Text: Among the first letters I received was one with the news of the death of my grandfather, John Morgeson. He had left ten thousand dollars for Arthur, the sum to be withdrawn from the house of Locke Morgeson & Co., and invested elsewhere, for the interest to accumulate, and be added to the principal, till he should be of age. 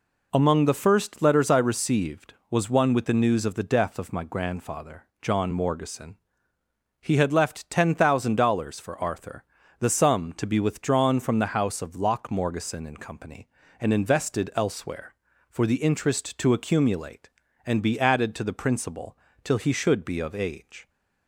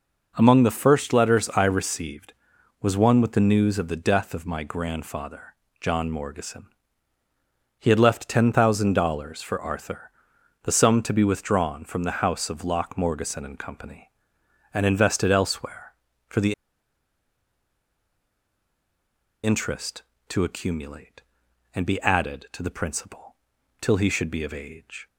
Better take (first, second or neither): first